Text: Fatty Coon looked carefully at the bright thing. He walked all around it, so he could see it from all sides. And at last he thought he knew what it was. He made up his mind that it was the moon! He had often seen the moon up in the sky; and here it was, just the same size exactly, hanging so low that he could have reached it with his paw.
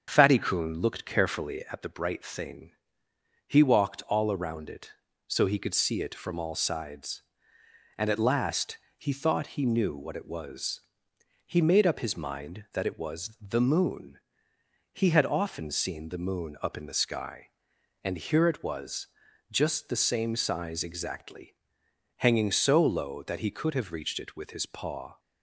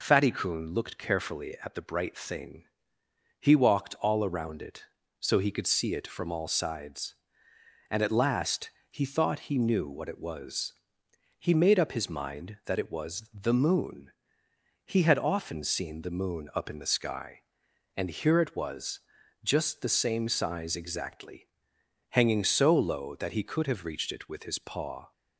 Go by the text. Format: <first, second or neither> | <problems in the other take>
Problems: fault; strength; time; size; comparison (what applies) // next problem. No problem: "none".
second | starts louder than the rest; strong; until 1.9 s; 7 dB // pauses between "last" and "he"; slight; at 8.7 s; 0.18 s long; slight in the second